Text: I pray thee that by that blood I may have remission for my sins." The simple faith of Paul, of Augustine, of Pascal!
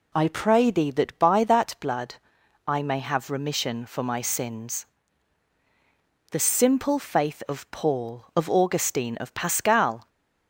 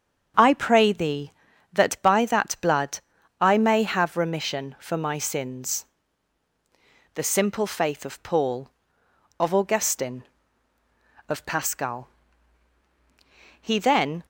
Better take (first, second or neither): first